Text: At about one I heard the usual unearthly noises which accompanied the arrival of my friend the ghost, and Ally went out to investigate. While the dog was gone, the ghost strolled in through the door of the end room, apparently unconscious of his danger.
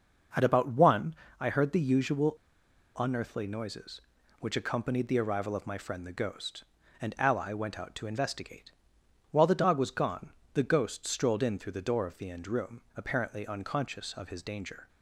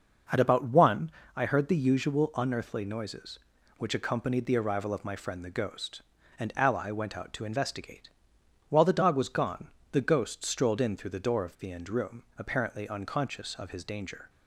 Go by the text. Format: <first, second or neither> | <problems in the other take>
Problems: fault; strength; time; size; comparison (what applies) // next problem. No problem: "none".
second | pauses between "one" and "I"; slight; at 1.1 s; 0.26 s long; slight in the second // pauses between "usual" and "unearthly"; noticeable; at 2.3 s; 0.62 s long